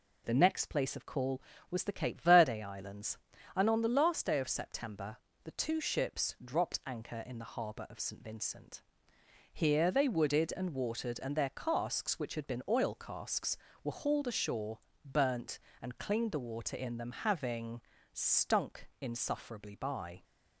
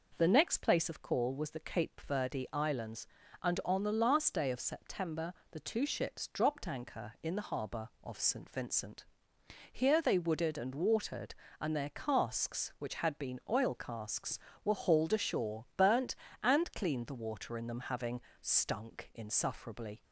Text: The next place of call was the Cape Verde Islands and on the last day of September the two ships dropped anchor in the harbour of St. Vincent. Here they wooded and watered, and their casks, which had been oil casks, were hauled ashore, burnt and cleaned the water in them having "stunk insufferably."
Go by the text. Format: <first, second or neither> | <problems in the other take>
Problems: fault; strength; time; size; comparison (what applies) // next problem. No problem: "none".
second | pauses between "September" and "the"; slight; at 5.1 s; 0.26 s long; slight in the second // pauses between "having" and "stunk"; slight; at 17.8 s; 0.30 s long; slight in the second // goes on to say "By"; slight; from 19.7 s on; 0.48 s long